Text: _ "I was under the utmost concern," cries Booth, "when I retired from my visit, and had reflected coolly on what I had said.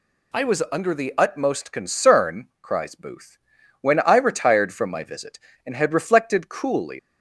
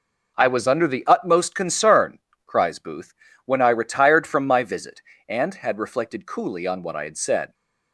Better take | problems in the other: second | stops before "on what I had said"; at 6.9 s

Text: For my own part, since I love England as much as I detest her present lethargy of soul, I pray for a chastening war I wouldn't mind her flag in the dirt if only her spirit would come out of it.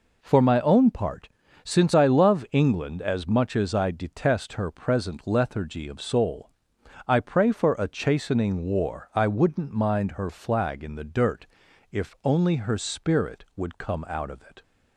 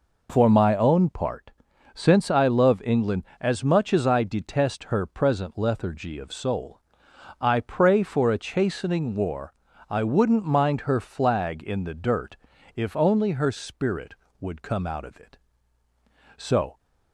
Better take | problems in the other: first | pauses between "war" and "I"; slight; at 9.5 s; 0.34 s long // pauses between "dirt" and "if"; at 12.3 s; 0.38 s long; also in the first // goes on to say "So"; slight; from 16.3 s on; 0.42 s long

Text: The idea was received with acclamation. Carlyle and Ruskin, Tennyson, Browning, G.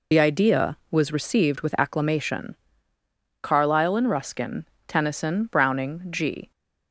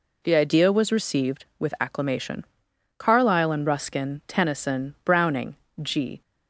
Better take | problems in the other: second | loses the start of "The"; at 0.1 s; 50 ms

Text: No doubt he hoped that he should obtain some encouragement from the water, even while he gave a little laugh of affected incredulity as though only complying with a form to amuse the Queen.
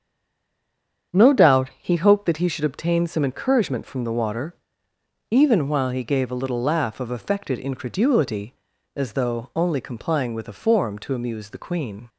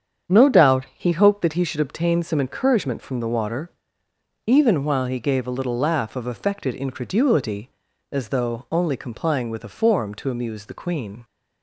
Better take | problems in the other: second | stays silent before the first word; until 1.1 s; 1.1 s long // starts louder than the rest; strong; until 2.2 s; 8 dB; strong in the second

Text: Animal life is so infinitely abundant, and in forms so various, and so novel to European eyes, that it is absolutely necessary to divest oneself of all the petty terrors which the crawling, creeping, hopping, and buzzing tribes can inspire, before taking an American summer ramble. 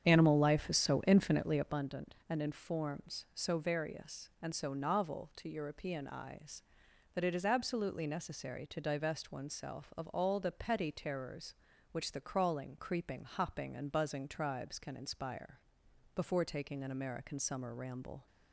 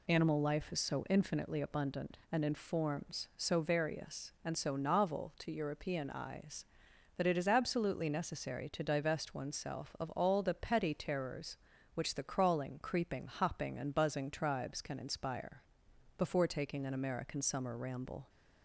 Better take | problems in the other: second | starts louder than the rest; strong; until 1.9 s; 8.5 dB

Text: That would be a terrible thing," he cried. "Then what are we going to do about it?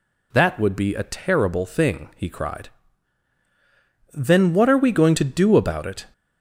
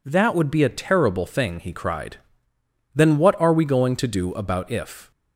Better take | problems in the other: first | says "if" for "it"; at 4.7 s

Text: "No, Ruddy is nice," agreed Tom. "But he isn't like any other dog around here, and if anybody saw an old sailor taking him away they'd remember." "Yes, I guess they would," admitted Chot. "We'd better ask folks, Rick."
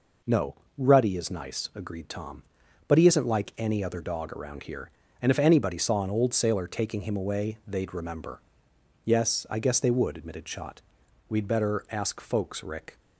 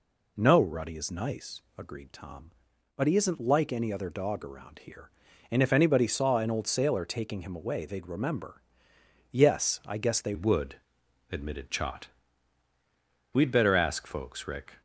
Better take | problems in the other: first | changes voice at "would"; from 10.3 s on; 4.5 s long

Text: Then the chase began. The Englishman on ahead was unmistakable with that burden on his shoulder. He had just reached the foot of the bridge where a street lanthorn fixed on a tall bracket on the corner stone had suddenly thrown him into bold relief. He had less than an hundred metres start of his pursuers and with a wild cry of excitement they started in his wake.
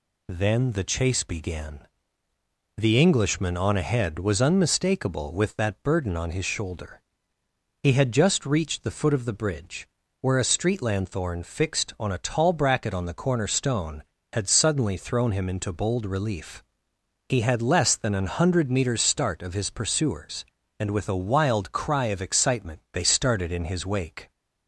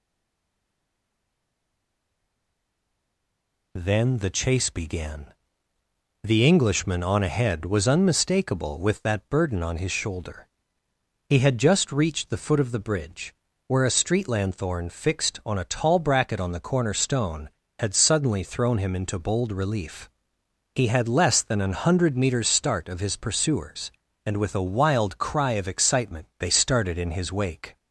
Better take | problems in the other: first | stays silent before the first word; strong; until 3.7 s; 3.7 s long // pauses between "bridge" and "where"; slight; at 13.3 s; 0.36 s long; slight in the first

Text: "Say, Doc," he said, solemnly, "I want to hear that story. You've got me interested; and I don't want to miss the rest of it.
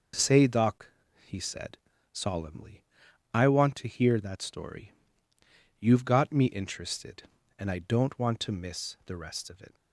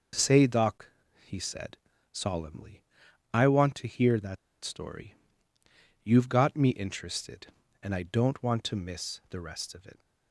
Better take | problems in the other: first | pauses between "that" and "story"; slight; at 4.3 s; 0.26 s long

